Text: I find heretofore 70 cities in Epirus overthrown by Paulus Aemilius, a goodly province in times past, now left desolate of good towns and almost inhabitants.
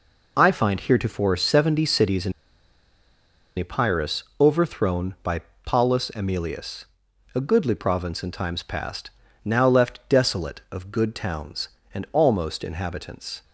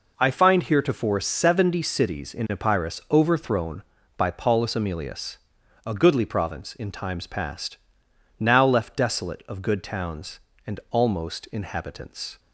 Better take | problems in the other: second | pauses between "in" and "Epirus"; strong; at 2.3 s; 1.2 s long // pauses between "Epirus" and "overthrown"; slight; at 4.2 s; 0.16 s long // pauses between "by" and "Paulus"; slight; at 5.3 s; 0.26 s long

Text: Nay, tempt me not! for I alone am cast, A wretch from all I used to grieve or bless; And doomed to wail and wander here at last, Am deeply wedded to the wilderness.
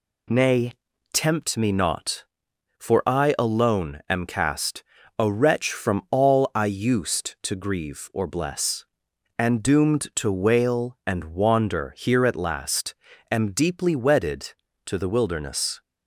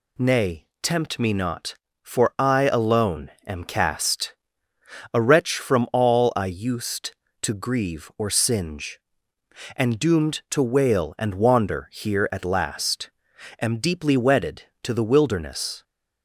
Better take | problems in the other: first | pauses between "alone" and "am"; slight; at 3.2 s; 0.16 s long // says "singe" for "bless"; at 8.3 s

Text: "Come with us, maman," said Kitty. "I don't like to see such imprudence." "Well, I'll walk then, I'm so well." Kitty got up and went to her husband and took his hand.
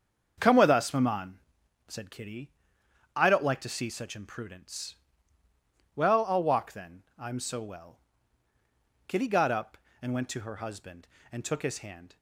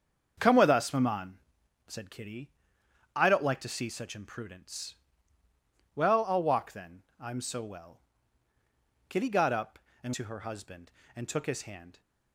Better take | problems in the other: first | starts louder than the rest; until 1.3 s; 7 dB; also in the first // skips "went"; at 10.1 s

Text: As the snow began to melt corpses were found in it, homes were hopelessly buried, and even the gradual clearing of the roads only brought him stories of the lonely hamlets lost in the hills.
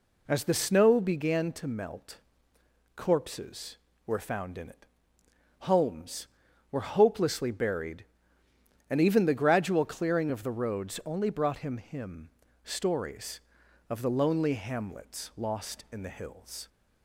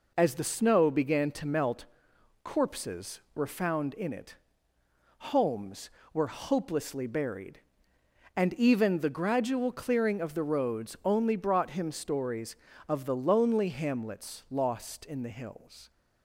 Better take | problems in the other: second | pauses between "melt" and "corpses"; noticeable; at 2.1 s; 0.76 s long; noticeable in the second // says "him" twice; at 11.7 s

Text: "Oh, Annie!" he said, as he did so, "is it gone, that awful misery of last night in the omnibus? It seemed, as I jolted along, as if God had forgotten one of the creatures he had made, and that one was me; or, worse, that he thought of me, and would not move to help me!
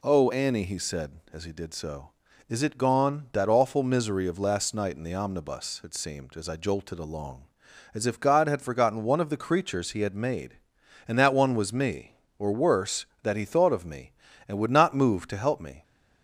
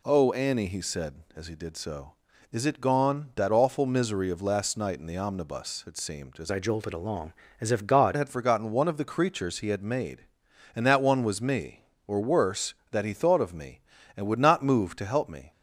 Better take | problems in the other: first | changes voice from "I" to "God"; from 6.4 to 8.1 s; 1.7 s long

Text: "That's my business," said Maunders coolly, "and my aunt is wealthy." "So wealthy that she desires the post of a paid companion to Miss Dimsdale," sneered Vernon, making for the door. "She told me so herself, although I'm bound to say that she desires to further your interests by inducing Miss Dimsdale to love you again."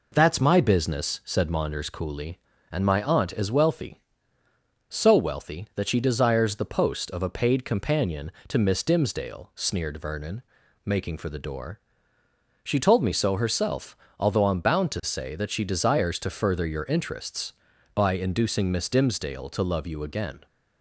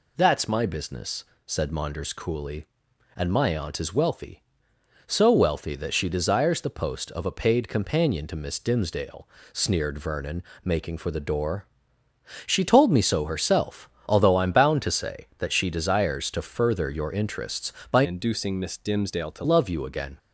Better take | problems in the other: first | changes voice from "inducing" to "to"; from 18.0 to 19.4 s; 1.4 s long

